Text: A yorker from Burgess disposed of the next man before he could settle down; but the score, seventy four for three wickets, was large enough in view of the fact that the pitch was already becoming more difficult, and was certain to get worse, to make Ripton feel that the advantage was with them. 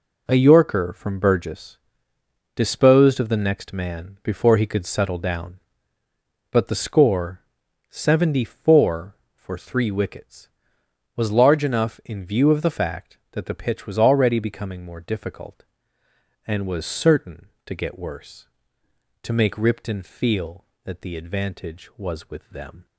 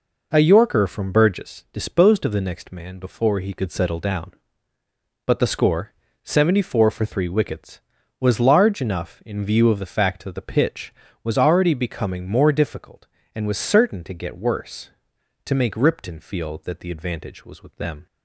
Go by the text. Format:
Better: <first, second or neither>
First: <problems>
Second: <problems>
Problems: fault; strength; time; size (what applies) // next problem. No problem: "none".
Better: second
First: gets quieter; strong; throughout; 10 dB // pauses between "Burgess" and "disposed"; noticeable; at 1.7 s; 0.76 s long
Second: none